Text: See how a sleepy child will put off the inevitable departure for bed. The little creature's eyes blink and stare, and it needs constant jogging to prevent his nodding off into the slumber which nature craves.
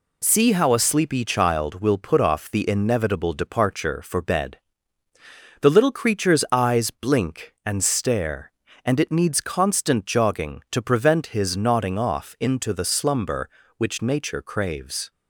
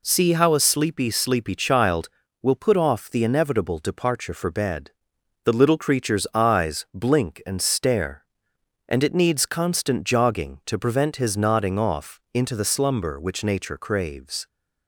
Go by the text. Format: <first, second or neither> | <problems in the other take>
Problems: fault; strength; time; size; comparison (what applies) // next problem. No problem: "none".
first | says "sleepy" twice; at 1.1 s